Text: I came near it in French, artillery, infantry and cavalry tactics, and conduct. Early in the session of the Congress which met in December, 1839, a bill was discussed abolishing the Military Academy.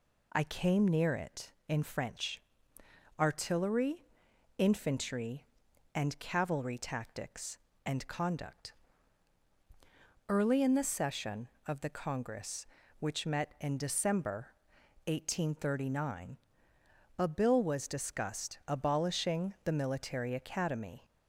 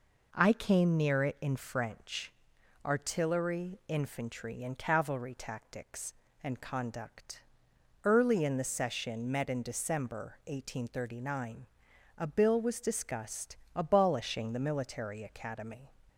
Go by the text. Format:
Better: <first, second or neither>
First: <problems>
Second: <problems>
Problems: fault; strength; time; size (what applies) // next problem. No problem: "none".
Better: first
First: none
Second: skips "of the Congress which"; at 9.2 s // pauses between "discussed" and "abolishing"; slight; at 13.5 s; 0.18 s long